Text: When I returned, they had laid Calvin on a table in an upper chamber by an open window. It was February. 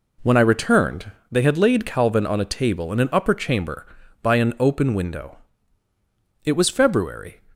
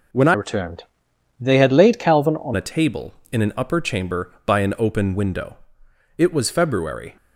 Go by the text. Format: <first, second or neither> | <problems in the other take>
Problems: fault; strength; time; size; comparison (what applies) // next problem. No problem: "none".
first | changes voice from "returned" to "on"; from 0.3 to 2.5 s; 2.2 s long